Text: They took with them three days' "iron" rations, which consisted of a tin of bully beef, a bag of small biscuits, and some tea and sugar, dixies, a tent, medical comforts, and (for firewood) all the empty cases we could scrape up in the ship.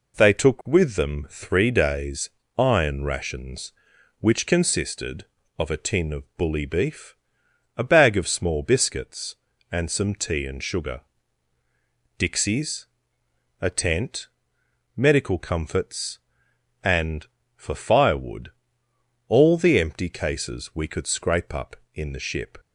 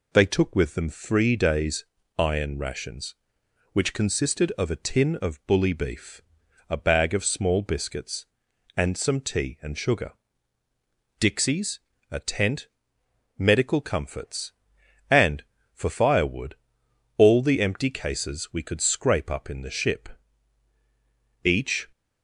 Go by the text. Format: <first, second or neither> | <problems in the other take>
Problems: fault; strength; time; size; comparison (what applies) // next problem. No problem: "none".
first | pauses between "days" and "iron"; slight; at 1.8 s; 0.32 s long; slight in the first // goes on to say "Each"; slight; from 21.4 s on; 0.48 s long